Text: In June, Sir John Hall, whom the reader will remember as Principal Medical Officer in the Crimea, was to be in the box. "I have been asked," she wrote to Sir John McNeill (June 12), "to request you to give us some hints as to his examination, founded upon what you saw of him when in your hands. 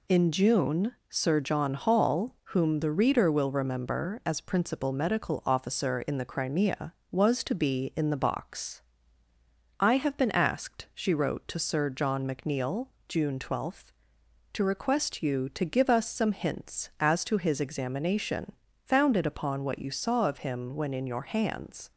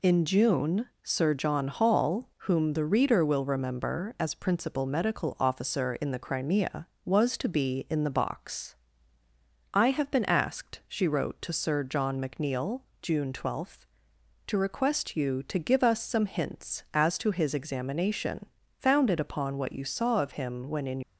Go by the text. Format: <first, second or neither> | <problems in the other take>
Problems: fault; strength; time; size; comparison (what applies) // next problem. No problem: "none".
first | stops before "your hands"; at 21.0 s